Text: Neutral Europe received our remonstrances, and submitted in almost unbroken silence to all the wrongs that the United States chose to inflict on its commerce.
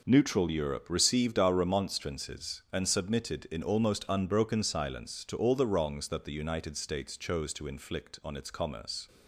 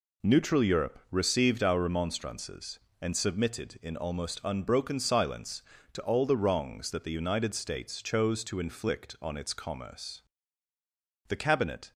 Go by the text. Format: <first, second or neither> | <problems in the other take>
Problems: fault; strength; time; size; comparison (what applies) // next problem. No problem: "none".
first | goes on to say "The Cabinet"; noticeable; from 11.2 s on; 0.64 s long